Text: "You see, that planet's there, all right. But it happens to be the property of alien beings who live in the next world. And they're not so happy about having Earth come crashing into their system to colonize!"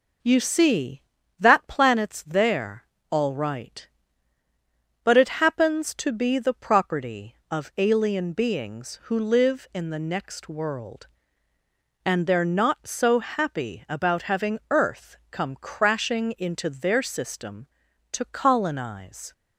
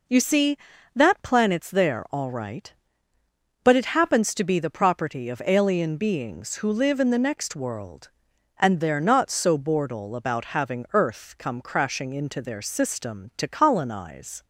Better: first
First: none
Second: says "bordel" for "happy"; at 9.5 s

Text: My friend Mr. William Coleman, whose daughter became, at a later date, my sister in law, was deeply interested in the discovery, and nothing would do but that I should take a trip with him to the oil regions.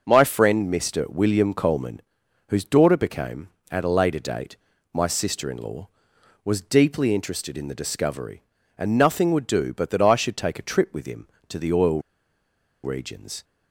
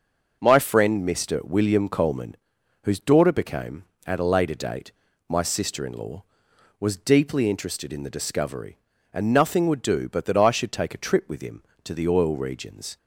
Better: second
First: starts louder than the rest; until 1.0 s; 6 dB // pauses between "oil" and "regions"; noticeable; at 12.0 s; 0.82 s long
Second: starts louder than the rest; noticeable; until 1.4 s; 6 dB

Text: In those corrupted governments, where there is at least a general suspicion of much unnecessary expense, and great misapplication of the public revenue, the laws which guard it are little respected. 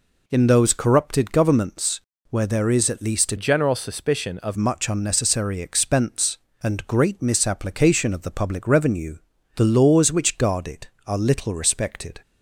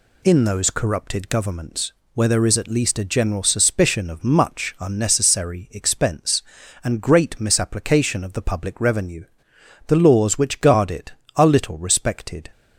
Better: second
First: changes voice from "general" to "of"; from 3.3 to 4.5 s; 1.2 s long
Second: none

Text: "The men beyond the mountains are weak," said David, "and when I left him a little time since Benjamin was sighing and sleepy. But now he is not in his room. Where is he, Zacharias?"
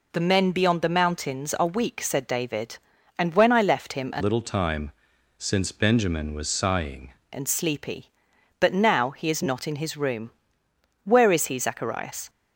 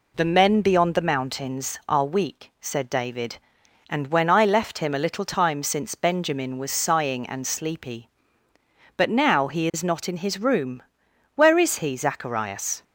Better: second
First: changes voice from "little" to "sighing"; from 4.1 to 7.1 s; 3.0 s long // pauses between "time" and "since"; noticeable; at 4.9 s; 0.46 s long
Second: none

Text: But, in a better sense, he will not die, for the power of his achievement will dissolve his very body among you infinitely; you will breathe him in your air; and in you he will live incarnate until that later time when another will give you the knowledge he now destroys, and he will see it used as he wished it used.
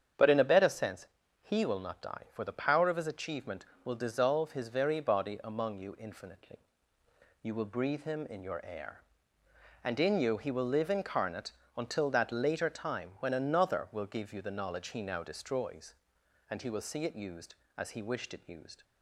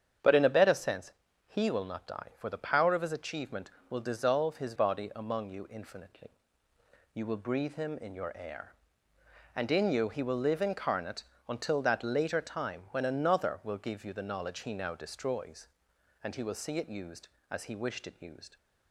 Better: first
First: starts louder than the rest; strong; until 1.5 s; 8.5 dB // pauses between "incarnate" and "until"; slight; at 11.5 s; 0.26 s long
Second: starts louder than the rest; strong; until 1.5 s; 8.5 dB // skips "very"; at 4.7 s // pauses between "incarnate" and "until"; slight; at 11.2 s; 0.26 s long

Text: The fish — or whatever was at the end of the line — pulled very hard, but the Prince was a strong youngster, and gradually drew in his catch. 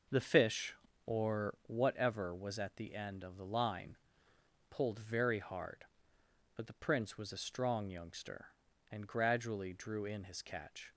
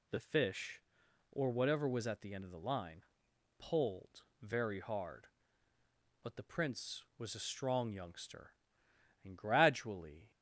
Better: first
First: none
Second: pauses between "pulled" and "very"; slight; at 4.2 s; 0.18 s long // stops before "drew in his catch"; at 10.3 s

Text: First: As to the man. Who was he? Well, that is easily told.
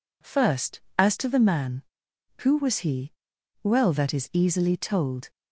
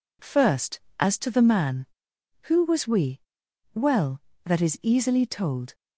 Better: first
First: none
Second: says "we" for "he"; at 2.8 s

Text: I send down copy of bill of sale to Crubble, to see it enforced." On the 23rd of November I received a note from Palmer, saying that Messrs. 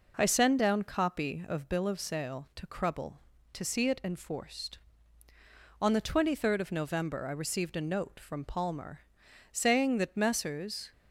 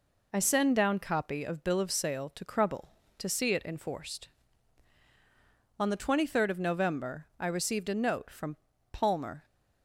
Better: first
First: none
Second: pauses between "from" and "Palmer"; slight; at 8.5 s; 0.36 s long // stops before "saying that Messrs"; at 9.4 s

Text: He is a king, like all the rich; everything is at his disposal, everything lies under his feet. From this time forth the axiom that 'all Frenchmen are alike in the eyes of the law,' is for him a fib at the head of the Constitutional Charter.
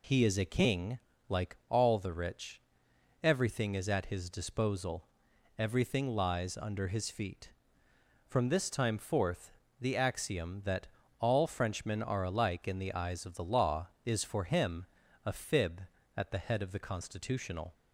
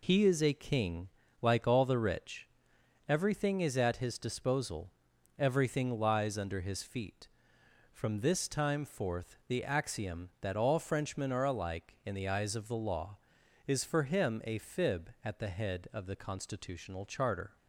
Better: second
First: pauses between "forth" and "the"; slight; at 9.4 s; 0.32 s long // pauses between "that" and "all"; slight; at 10.8 s; 0.34 s long // pauses between "him" and "a"; at 14.8 s; 0.40 s long // stops before "Charter"; at 17.7 s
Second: none

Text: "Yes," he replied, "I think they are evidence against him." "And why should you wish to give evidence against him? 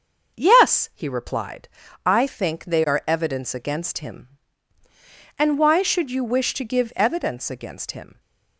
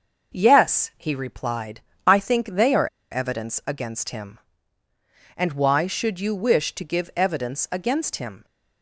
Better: first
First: starts louder than the rest; until 1.4 s; 6 dB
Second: starts louder than the rest; noticeable; until 1.4 s; 6 dB // pauses between "are" and "evidence"; slight; at 2.8 s; 0.24 s long

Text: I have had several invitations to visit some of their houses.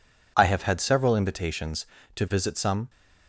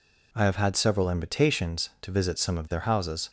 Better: second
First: stops before "of their houses"; at 2.8 s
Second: none

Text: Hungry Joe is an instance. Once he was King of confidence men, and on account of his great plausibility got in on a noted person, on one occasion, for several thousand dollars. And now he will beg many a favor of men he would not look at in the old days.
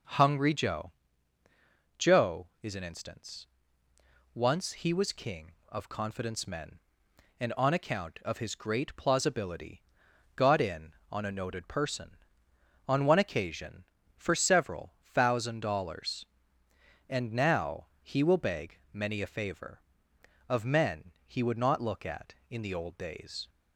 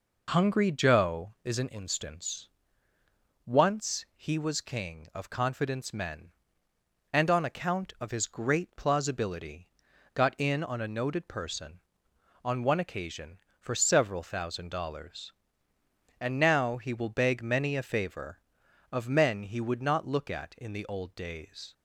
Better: second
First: says "Joe" twice; at 1.9 s // pauses between "plausibility" and "got"; noticeable; at 9.8 s; 0.56 s long // pauses between "beg" and "many"; slight; at 18.7 s; 0.16 s long // pauses between "men" and "he"; slight; at 21.1 s; 0.16 s long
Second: pauses between "plausibility" and "got"; at 9.6 s; 0.44 s long

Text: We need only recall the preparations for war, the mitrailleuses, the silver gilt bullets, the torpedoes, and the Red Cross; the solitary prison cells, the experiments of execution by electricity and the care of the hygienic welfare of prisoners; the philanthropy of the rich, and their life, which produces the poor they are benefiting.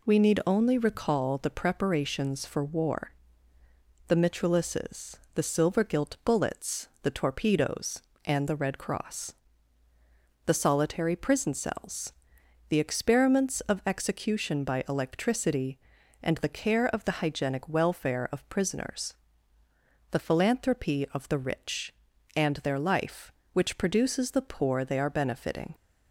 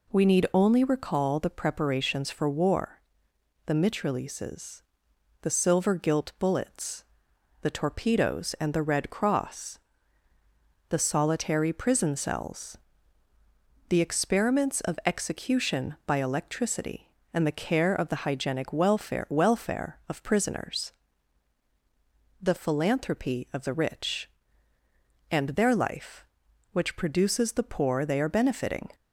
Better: first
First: none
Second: says "welfare" twice; at 19.2 s

